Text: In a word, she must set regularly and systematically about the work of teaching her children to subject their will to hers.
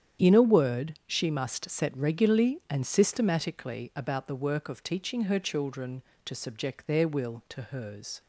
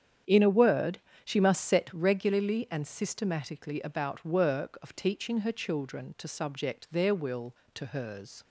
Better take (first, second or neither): first